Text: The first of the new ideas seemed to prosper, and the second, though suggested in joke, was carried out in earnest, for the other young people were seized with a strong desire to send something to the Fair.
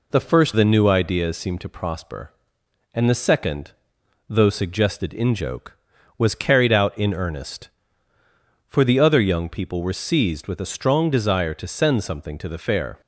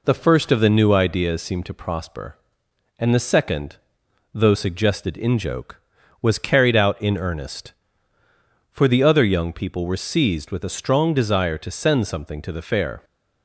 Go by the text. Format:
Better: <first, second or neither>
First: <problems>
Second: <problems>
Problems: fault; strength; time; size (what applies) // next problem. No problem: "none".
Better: second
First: skips "of"; at 0.5 s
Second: none